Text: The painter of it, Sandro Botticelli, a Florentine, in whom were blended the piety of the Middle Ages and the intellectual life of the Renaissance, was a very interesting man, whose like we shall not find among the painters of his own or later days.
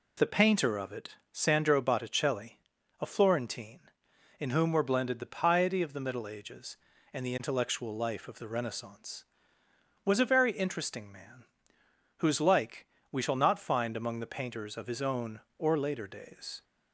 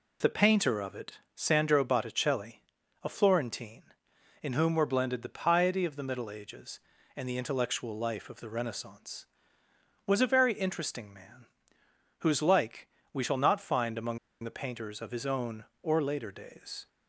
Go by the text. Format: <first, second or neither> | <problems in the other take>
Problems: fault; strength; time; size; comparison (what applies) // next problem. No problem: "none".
first | pauses between "like" and "we"; slight; at 12.8 s; 0.26 s long; slight in the first // pauses between "among" and "the"; slight; at 14.1 s; 0.25 s long